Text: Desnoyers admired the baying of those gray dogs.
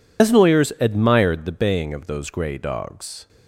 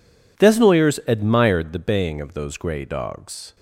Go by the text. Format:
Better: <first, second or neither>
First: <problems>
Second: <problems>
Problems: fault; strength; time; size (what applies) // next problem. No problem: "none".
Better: second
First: loses the start of "Desnoyers"; at 0.1 s; 100 ms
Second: none